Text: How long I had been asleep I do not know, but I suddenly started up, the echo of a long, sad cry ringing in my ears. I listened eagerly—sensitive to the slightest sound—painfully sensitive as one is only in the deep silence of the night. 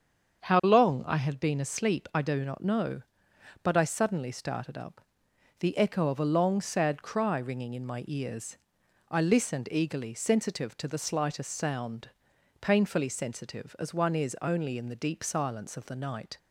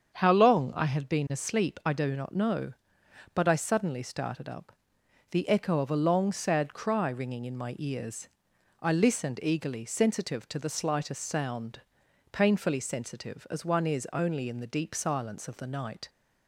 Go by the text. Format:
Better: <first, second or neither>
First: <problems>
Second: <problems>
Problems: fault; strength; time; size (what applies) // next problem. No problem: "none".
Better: neither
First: starts louder than the rest; strong; until 1.4 s; 7 dB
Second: starts louder than the rest; strong; until 1.1 s; 7.5 dB